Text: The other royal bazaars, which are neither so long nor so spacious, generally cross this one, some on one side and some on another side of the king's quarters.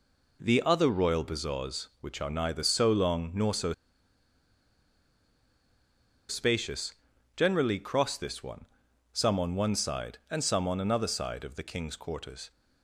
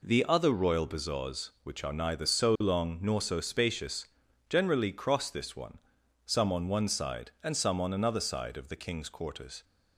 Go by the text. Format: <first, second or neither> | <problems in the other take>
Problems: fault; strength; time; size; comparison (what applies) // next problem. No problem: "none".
second | pauses between "so" and "spacious"; strong; at 3.7 s; 2.5 s long